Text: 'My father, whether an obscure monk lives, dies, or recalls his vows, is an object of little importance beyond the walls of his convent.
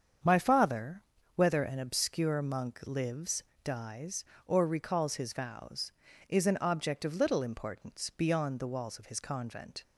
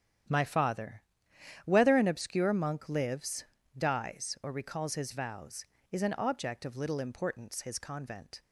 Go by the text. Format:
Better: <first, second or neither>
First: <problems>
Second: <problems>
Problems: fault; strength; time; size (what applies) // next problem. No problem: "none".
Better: first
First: starts louder than the rest; strong; until 1.5 s; 7.5 dB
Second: starts louder than the rest; strong; until 1.9 s; 9.5 dB // skips "beyond the walls of"; at 7.6 s